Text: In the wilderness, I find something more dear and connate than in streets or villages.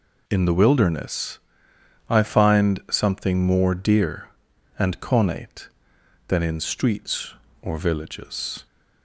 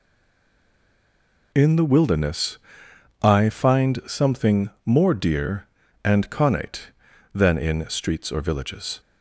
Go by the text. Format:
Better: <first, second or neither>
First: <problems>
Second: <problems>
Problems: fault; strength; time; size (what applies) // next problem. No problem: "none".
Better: first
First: none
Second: stays silent before the first word; noticeable; until 1.5 s; 1.5 s long // pauses between "something" and "more"; slight; at 4.6 s; 0.16 s long